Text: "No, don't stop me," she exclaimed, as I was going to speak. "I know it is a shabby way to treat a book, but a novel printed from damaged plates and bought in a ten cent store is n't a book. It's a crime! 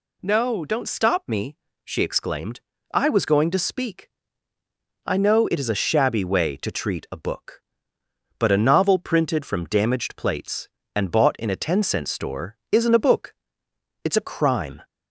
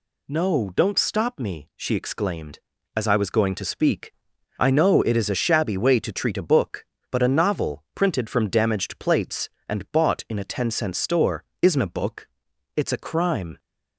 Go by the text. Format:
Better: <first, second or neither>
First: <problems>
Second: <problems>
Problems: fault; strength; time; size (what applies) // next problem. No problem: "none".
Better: second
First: skips "as"; at 2.7 s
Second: none